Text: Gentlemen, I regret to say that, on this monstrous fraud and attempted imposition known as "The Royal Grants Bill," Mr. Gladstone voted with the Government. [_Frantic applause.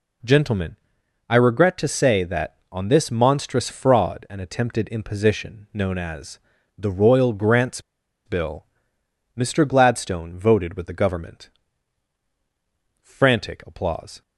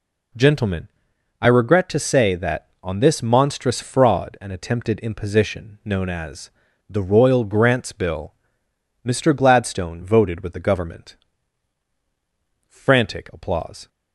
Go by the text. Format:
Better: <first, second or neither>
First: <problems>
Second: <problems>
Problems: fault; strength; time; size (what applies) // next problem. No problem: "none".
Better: second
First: pauses between "as" and "The"; at 6.3 s; 0.40 s long // pauses between "Grants" and "Bill"; at 7.8 s; 0.45 s long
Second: pauses between "as" and "The"; at 6.4 s; 0.40 s long